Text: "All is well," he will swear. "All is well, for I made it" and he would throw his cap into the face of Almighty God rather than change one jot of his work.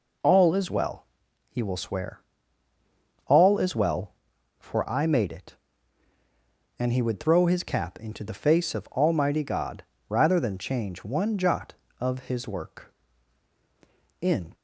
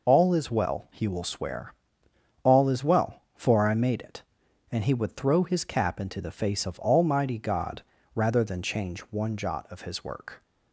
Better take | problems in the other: second | pauses between "God" and "rather"; slight; at 9.8 s; 0.28 s long; slight in the second // goes on to say "In"; slight; from 14.1 s on; 0.34 s long

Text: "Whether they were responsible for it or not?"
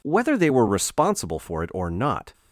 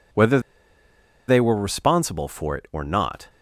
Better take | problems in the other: first | pauses between "Whether" and "they"; noticeable; at 0.4 s; 0.87 s long

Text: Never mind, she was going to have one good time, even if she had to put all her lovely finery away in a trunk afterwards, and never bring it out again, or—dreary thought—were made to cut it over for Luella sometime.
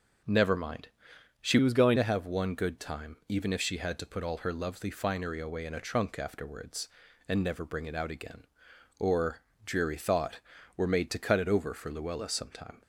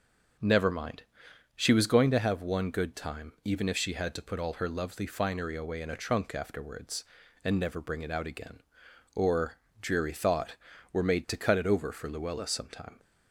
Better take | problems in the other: second | starts louder than the rest; until 1.8 s; 6 dB // changes voice from "was" to "going"; from 1.6 to 1.9 s; 0.3 s long

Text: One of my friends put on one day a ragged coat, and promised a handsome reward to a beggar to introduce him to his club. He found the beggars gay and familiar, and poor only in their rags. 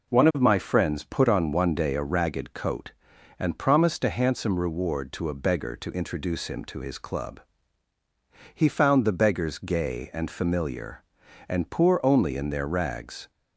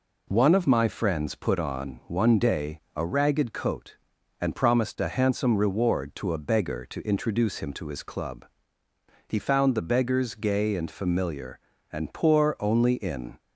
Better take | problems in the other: first | stops before "their rags"; at 13.4 s

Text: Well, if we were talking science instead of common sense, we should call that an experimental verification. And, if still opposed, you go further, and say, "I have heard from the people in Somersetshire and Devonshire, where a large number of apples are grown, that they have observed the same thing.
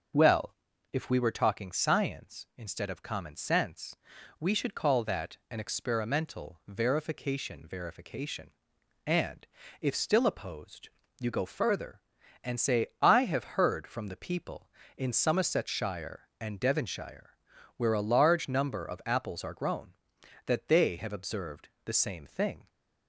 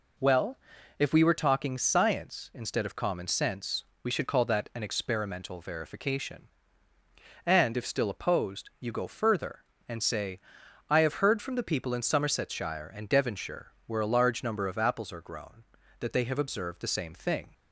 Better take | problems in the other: second | starts louder than the rest; until 1.5 s; 6.5 dB // says "verification" twice; at 7.6 s // pauses between "observed" and "the"; slight; at 21.7 s; 0.16 s long

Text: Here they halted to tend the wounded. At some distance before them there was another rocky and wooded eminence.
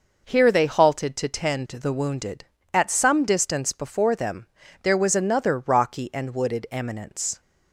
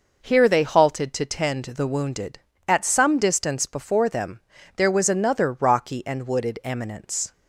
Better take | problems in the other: neither | pauses between "them" and "there"; slight; the same in both

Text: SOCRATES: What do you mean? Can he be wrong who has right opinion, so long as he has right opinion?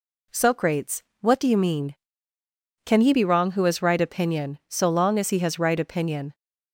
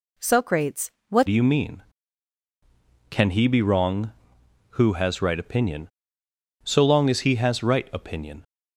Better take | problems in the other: first | changes voice at "do"; from 1.2 s on; 7.2 s long

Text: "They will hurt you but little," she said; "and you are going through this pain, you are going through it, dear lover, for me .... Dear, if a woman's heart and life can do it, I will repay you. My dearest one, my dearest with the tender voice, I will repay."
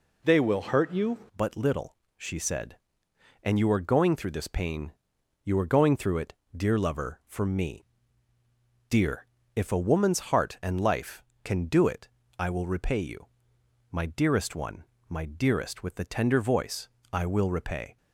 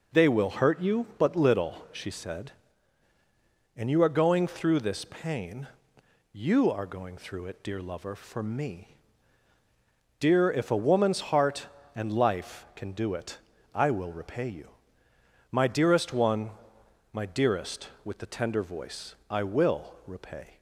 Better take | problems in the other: second | changes voice at "but"; from 1.3 s on; 16.6 s long

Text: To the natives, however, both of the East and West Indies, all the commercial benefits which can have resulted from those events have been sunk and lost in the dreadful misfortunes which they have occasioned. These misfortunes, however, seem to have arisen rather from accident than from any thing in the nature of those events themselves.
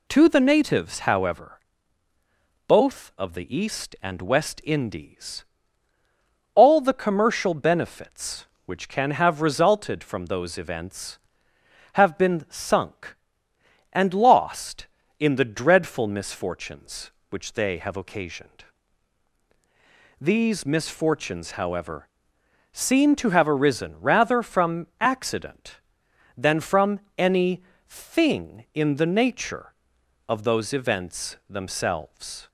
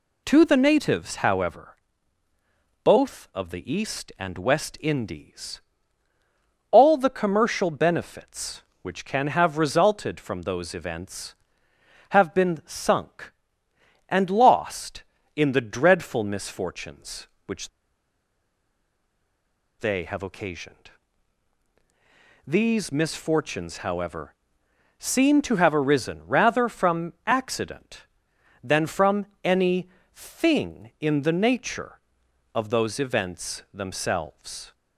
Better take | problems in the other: first | pauses between "which" and "they"; strong; at 17.6 s; 2.1 s long // pauses between "from" and "any"; slight; at 29.2 s; 0.16 s long; slight in the first // pauses between "any" and "thing"; slight; at 29.8 s; 0.28 s long; slight in the first

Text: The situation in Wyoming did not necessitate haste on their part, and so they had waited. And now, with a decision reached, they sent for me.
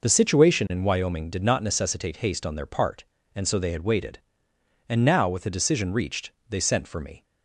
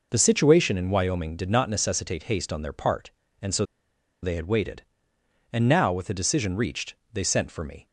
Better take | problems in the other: first | pauses between "so" and "they"; noticeable; at 3.6 s; 0.59 s long

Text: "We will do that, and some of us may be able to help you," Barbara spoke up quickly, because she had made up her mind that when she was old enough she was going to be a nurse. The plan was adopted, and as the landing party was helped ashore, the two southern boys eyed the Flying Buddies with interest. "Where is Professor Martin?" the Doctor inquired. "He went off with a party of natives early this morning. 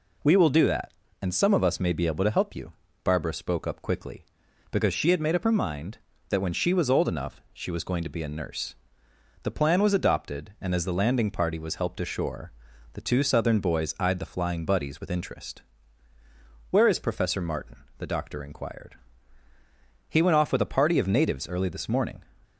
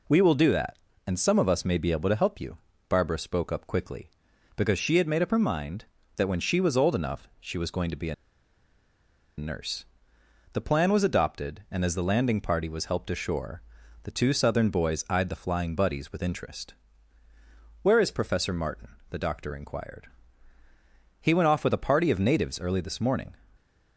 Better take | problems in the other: first | pauses between "a" and "nurse"; at 8.1 s; 1.2 s long

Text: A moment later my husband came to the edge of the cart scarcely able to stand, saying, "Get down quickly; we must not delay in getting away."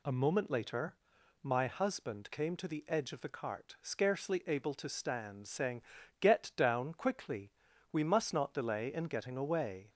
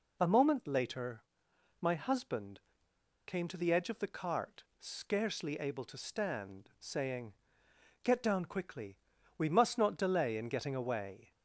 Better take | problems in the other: first | pauses between "later" and "my"; noticeable; at 1.2 s; 0.58 s long; noticeable in the first // pauses between "husband" and "came"; noticeable; at 2.5 s; 0.66 s long // pauses between "cart" and "scarcely"; slight; at 4.6 s; 0.16 s long

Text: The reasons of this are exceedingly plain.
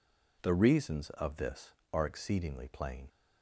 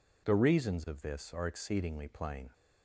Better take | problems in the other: neither | none

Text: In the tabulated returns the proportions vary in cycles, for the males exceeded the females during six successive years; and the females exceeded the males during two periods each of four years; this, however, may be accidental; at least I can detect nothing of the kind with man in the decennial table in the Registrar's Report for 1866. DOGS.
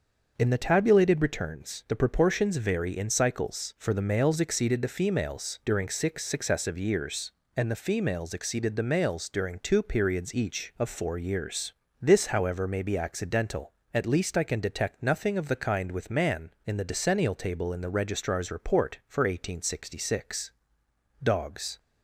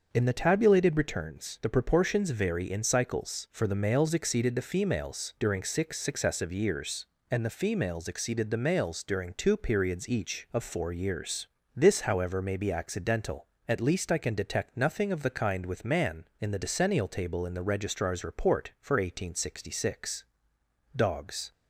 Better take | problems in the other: neither | starts louder than the rest; the same in both

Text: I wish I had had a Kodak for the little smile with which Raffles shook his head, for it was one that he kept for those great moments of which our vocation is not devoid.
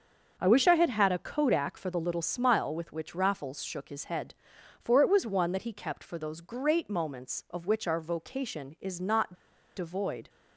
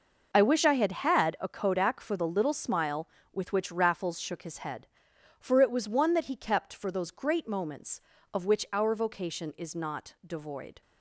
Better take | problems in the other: second | starts louder than the rest; until 1.4 s; 6.5 dB // pauses between "not" and "devoid"; at 9.3 s; 0.42 s long

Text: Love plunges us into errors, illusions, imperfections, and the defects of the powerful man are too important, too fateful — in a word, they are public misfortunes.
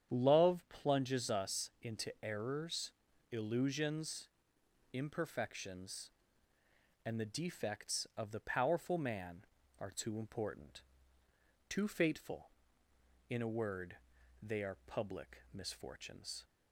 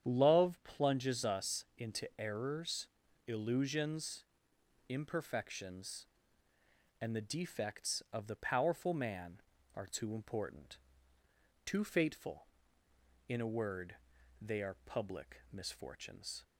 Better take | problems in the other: neither | starts louder than the rest; strong; the same in both

